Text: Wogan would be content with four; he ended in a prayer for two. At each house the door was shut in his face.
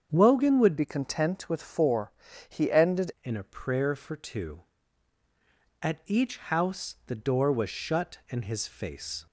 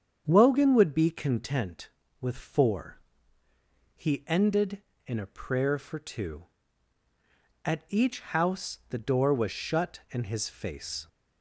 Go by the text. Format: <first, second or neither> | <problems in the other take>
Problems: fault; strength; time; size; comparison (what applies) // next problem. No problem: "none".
second | starts louder than the rest; strong; until 1.1 s; 7 dB; strong in the second // changes voice from "be" to "ended"; from 0.7 to 3.1 s; 2.4 s long